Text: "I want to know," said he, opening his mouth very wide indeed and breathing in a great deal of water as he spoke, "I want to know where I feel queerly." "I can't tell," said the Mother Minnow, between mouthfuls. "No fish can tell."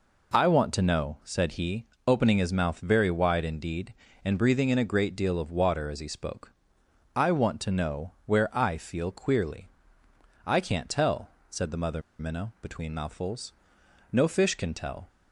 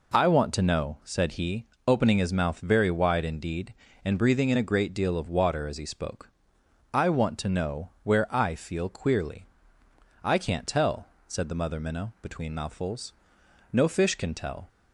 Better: second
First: pauses between "Mother" and "Minnow"; slight; at 12.0 s; 0.18 s long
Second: none

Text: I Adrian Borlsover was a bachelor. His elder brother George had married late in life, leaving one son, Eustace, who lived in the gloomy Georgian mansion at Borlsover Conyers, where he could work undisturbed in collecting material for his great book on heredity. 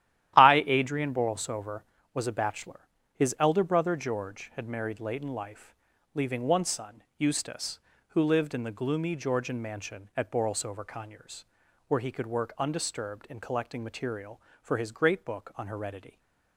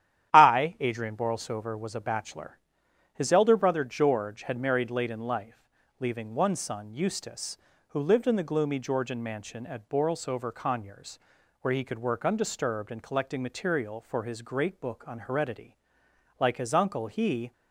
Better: first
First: starts louder than the rest; strong; until 1.3 s; 12.5 dB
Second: starts louder than the rest; strong; until 1.3 s; 11 dB // goes on to say "Like his uncle he"; noticeable; from 16.3 s on; 1.1 s long

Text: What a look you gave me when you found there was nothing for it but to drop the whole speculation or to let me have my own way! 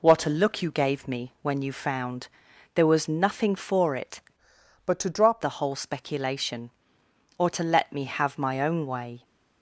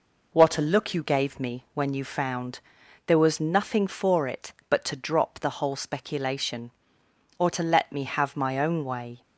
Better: second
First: pauses between "found" and "there"; noticeable; at 2.2 s; 0.46 s long // changes voice from "but" to "drop"; from 4.8 to 5.4 s; 0.6 s long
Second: pauses between "found" and "there"; noticeable; at 2.5 s; 0.46 s long

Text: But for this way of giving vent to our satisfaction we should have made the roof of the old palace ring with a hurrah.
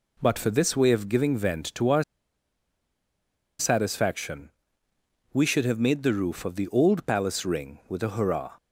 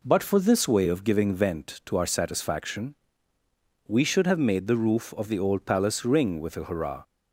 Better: second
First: pauses between "our" and "satisfaction"; strong; at 2.0 s; 1.5 s long // pauses between "satisfaction" and "we"; noticeable; at 4.4 s; 0.84 s long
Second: pauses between "satisfaction" and "we"; noticeable; at 2.9 s; 0.92 s long

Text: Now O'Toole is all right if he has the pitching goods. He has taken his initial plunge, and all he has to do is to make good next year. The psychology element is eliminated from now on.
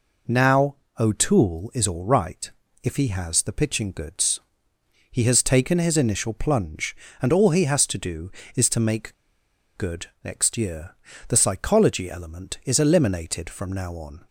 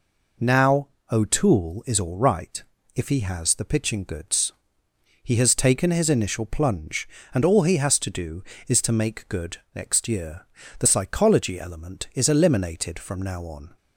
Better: second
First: pauses between "Now" and "O'Toole"; slight; at 0.7 s; 0.24 s long // pauses between "right" and "if"; slight; at 2.5 s; 0.32 s long // pauses between "make" and "good"; noticeable; at 9.1 s; 0.62 s long // pauses between "good" and "next"; slight; at 10.0 s; 0.16 s long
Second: pauses between "Now" and "O'Toole"; slight; at 0.8 s; 0.24 s long // pauses between "right" and "if"; slight; at 2.6 s; 0.32 s long // pauses between "good" and "next"; slight; at 9.5 s; 0.16 s long

